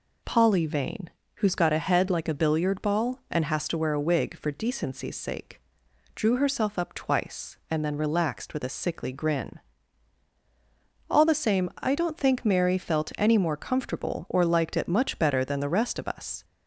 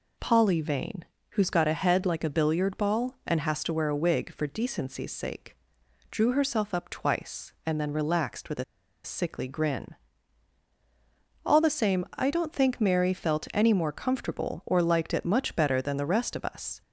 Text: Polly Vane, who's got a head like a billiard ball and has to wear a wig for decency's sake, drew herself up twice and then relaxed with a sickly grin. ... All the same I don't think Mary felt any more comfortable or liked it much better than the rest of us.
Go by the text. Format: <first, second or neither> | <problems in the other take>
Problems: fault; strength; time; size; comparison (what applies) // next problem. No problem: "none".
first | pauses between "a" and "sickly"; at 8.6 s; 0.40 s long